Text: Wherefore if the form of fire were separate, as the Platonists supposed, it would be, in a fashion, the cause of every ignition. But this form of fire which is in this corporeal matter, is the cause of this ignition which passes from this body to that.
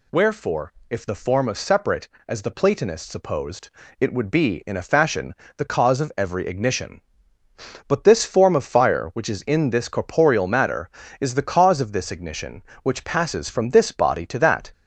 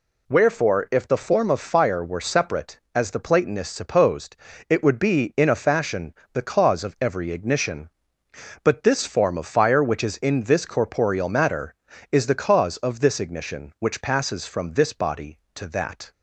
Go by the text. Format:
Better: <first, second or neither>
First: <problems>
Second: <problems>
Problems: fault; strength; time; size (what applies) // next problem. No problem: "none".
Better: second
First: pauses between "Wherefore" and "if"; slight; at 0.7 s; 0.16 s long // skips "fire were"; at 1.5 s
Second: none